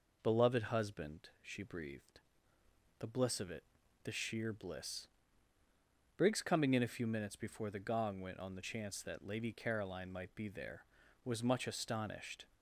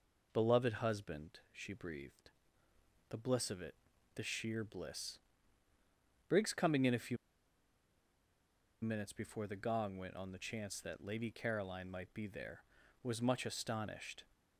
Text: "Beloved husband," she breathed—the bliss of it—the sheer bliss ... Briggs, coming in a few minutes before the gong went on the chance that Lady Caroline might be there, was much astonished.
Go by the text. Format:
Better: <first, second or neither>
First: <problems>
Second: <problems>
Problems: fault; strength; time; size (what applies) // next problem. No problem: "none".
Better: first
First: none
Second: pauses between "few" and "minutes"; strong; at 7.1 s; 1.6 s long